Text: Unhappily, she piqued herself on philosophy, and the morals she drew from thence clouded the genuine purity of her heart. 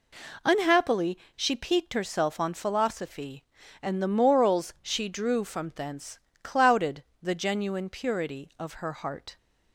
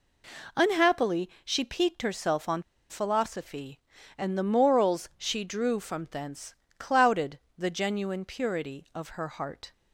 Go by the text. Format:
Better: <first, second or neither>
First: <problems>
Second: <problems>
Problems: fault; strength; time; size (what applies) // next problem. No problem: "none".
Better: first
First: pauses between "thence" and "clouded"; slight; at 6.1 s; 0.26 s long // pauses between "clouded" and "the"; slight; at 7.0 s; 0.18 s long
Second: pauses between "on" and "philosophy"; slight; at 2.6 s; 0.27 s long // pauses between "thence" and "clouded"; slight; at 6.5 s; 0.26 s long // pauses between "clouded" and "the"; slight; at 7.3 s; 0.18 s long